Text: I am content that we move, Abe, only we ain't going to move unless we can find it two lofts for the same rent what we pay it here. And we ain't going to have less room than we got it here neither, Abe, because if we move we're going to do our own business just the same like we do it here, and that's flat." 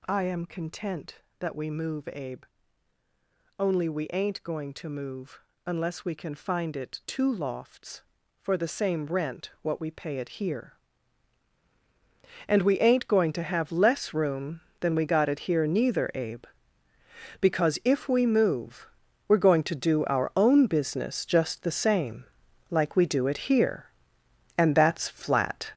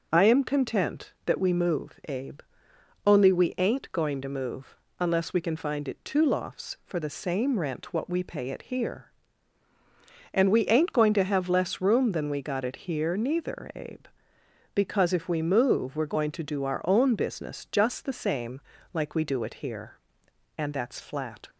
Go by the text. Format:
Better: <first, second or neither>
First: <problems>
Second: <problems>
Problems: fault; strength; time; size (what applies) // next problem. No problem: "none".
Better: second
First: gets louder; strong; throughout; 8.5 dB // pauses between "move" and "unless"; slight; at 5.3 s; 0.26 s long // pauses between "move" and "we're"; at 18.8 s; 0.42 s long // pauses between "same" and "like"; at 22.2 s; 0.44 s long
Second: pauses between "move" and "unless"; slight; at 4.7 s; 0.24 s long // pauses between "same" and "like"; slight; at 18.6 s; 0.32 s long